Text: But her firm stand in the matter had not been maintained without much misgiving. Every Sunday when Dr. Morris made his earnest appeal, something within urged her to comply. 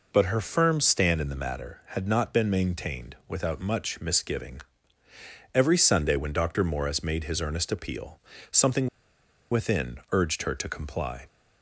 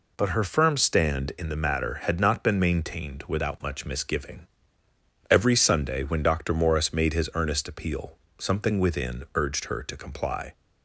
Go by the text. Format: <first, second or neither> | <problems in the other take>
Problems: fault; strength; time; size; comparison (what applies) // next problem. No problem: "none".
second | pauses between "something" and "within"; noticeable; at 8.8 s; 0.63 s long